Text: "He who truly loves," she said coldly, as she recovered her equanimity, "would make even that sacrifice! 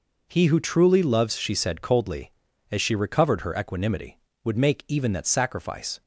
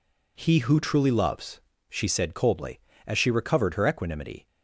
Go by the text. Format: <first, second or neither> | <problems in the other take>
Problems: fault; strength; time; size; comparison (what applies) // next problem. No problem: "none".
first | stops before "would make even that sacrifice"; at 4.4 s